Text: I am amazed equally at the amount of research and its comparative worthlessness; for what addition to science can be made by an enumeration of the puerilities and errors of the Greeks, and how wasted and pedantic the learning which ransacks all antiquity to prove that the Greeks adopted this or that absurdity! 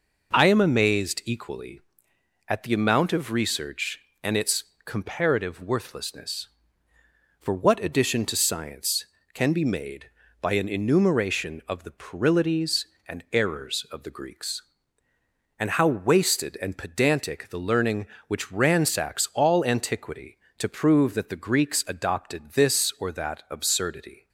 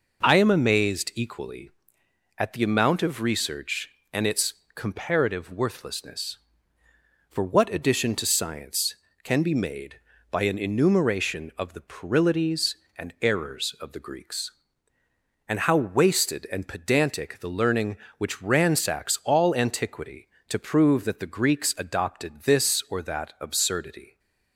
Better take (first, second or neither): neither